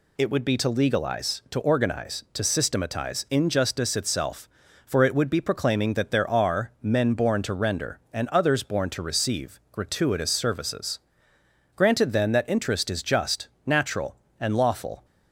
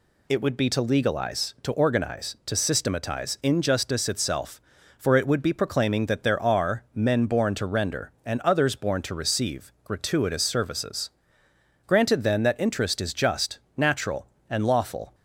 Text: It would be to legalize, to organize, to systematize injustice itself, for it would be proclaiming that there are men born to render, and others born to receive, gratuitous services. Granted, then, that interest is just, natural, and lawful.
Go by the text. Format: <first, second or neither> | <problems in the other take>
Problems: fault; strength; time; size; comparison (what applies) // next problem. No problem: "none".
neither | none